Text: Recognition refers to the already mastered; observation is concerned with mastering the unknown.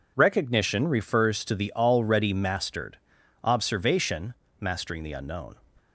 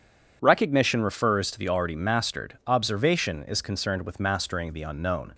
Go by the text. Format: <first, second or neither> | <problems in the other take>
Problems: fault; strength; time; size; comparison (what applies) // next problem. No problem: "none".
second | skips "is concerned with"; at 4.4 s